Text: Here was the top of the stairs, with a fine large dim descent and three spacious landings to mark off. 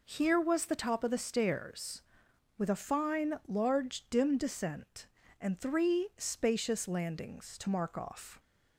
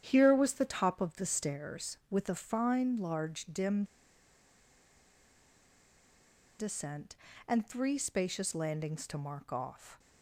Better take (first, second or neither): first